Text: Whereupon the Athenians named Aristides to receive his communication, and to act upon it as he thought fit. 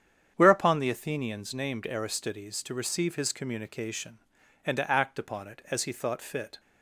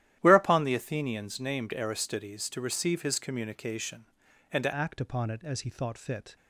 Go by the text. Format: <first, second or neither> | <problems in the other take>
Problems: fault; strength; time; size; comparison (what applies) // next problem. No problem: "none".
first | starts louder than the rest; strong; until 1.2 s; 12.5 dB; strong in the first // changes voice at "act"; from 4.7 s on; 1.6 s long